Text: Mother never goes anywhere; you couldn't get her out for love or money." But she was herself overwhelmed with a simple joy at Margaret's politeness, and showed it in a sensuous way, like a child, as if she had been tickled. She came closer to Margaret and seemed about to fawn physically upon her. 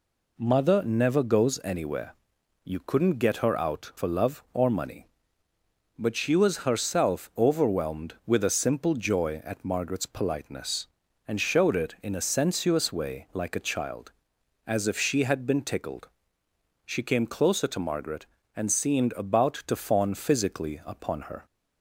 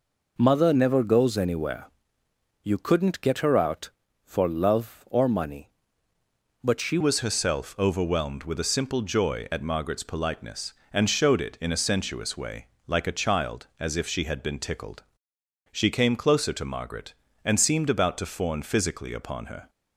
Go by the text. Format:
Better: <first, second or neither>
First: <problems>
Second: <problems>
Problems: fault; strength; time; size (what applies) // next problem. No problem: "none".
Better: first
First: none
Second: changes voice at "was"; from 7.0 s on; 12.6 s long